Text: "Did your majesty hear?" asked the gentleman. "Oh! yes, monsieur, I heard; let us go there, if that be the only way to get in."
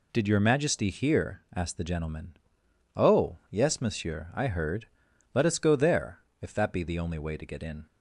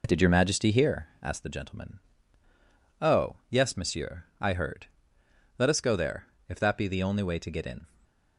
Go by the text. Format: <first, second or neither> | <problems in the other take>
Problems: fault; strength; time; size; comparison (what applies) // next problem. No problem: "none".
first | starts louder than the rest; noticeable; until 1.3 s; 4 dB // stays silent after the last word; slight; from 7.8 s on; 0.5 s long